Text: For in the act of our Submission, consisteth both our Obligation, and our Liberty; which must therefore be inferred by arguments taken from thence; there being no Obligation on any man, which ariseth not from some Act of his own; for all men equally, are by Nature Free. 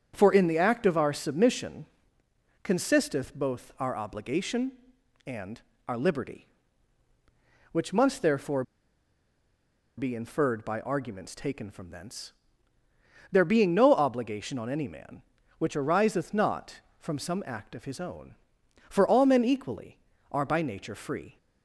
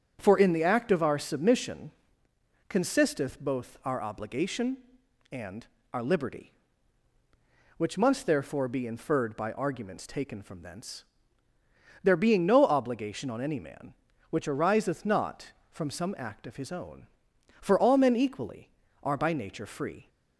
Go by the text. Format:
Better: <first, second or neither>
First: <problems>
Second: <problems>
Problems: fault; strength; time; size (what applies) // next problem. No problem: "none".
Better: second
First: starts louder than the rest; until 1.1 s; 7 dB // pauses between "and" and "our"; slight; at 5.6 s; 0.28 s long // pauses between "therefore" and "be"; strong; at 8.6 s; 1.3 s long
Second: starts louder than the rest; strong; until 1.2 s; 7 dB // pauses between "and" and "our"; slight; at 5.6 s; 0.28 s long